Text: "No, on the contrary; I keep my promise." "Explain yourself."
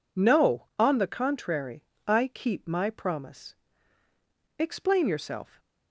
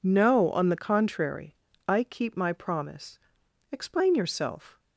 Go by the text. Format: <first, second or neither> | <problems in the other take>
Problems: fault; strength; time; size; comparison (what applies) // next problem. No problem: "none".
neither | none